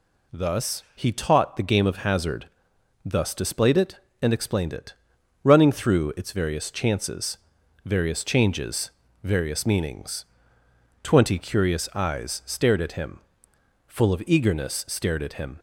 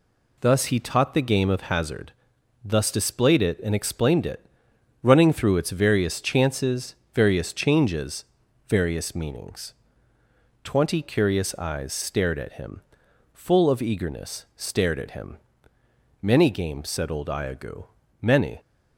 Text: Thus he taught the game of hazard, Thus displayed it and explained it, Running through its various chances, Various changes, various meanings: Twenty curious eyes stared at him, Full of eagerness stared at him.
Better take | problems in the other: first | goes on to say "Many games said old Iagoo Many"; strong; from 16.2 s on; 2.3 s long

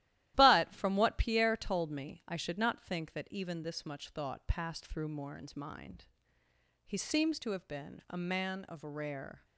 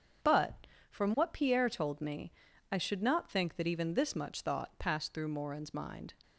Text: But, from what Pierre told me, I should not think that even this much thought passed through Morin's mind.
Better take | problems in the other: second | starts louder than the rest; strong; until 1.3 s; 14.5 dB; strong in the second // goes on to say "He seems to have been a man of rare"; strong; from 6.8 s on; 2.6 s long

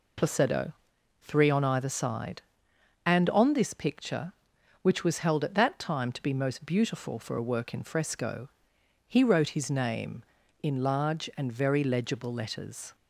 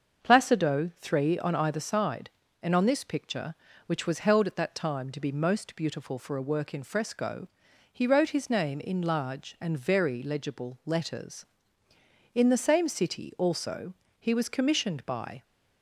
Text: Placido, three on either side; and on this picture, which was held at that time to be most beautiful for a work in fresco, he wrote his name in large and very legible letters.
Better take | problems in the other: first | starts louder than the rest; until 1.2 s; 6.5 dB // goes on to say "In the same city also he was commissioned by"; strong; from 12.3 s on; 3.0 s long

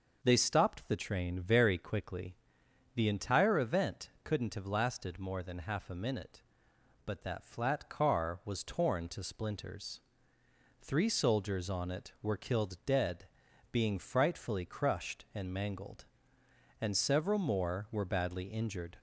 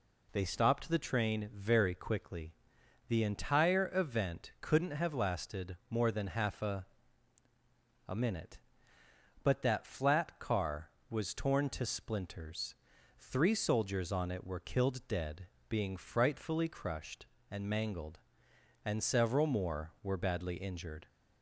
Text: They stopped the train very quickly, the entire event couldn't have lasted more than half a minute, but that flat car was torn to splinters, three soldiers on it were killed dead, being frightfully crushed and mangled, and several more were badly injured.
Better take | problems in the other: first | says "a" twice; at 8.0 s

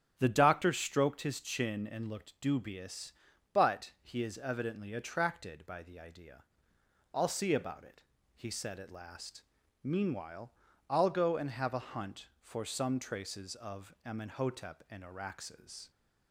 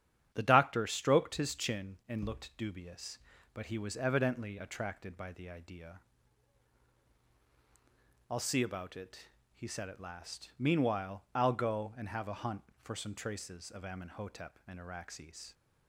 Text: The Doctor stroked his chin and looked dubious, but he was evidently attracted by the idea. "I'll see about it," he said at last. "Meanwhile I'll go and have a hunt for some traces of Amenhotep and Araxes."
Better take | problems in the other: second | starts louder than the rest; strong; until 1.1 s; 8.5 dB; strong in the second // says "is" for "was"; at 4.2 s // pauses between "Meanwhile" and "I'll"; slight; at 10.5 s; 0.34 s long

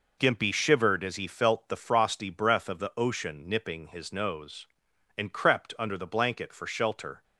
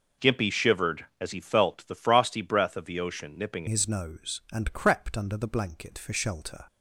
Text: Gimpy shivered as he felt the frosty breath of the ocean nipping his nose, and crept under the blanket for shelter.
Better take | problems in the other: first | changes voice at "his"; from 3.6 s on; 3.0 s long

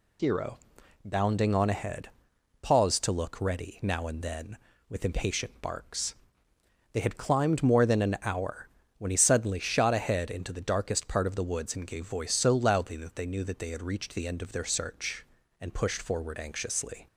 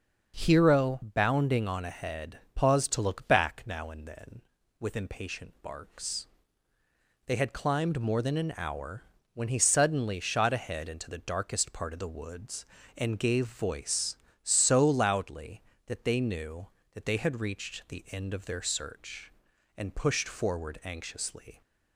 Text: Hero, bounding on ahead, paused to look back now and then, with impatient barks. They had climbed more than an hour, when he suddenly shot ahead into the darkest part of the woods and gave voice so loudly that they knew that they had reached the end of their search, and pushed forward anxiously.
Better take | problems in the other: second | says "ready" for "back"; at 3.4 s

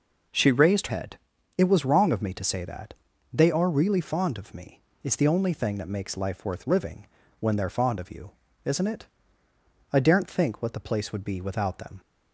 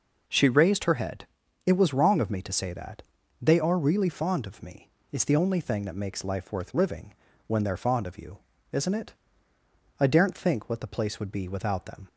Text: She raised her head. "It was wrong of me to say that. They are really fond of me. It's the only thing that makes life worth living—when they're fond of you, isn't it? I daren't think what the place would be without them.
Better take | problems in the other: second | skips "her"; at 0.8 s

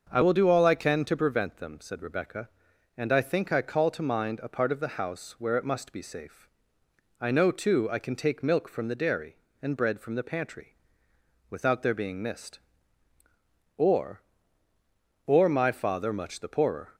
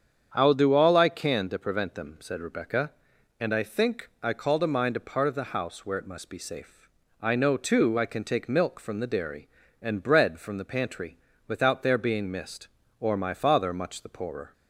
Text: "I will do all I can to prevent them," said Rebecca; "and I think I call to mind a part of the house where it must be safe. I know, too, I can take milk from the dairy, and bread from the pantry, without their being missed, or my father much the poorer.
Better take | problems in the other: second | starts louder than the rest; until 1.1 s; 6.5 dB; strong in the second // says "or" twice; at 15.2 s

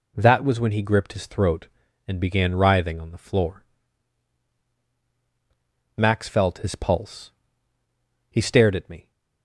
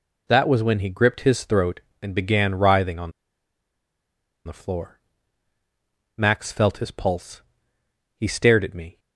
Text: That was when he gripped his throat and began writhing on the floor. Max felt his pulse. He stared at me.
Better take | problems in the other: first | pauses between "on" and "the"; strong; at 3.1 s; 1.3 s long

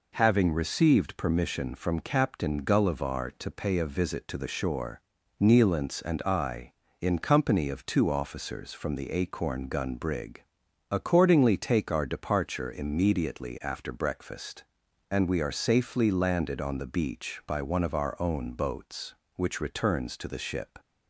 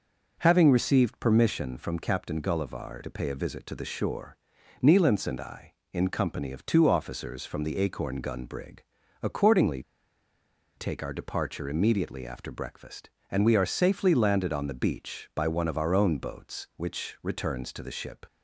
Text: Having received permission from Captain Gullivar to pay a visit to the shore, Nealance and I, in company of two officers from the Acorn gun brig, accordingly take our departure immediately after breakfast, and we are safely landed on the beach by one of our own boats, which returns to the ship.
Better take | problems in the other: first | pauses between "accordingly" and "take"; noticeable; at 9.8 s; 0.95 s long

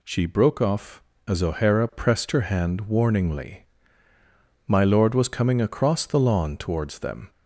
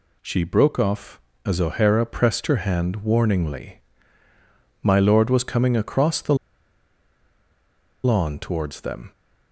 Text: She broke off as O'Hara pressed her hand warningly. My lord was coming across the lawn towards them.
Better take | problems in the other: first | pauses between "the" and "lawn"; strong; at 6.3 s; 1.6 s long

